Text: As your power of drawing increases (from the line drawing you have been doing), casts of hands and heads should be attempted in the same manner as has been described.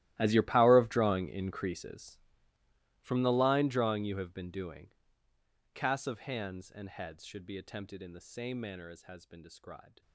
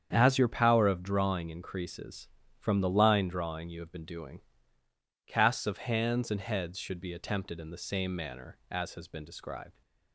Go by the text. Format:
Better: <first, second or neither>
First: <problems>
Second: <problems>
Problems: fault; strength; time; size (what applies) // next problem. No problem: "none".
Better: second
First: gets quieter; strong; throughout; 20.5 dB // starts louder than the rest; strong; until 1.1 s; 15 dB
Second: starts louder than the rest; strong; until 1.1 s; 8 dB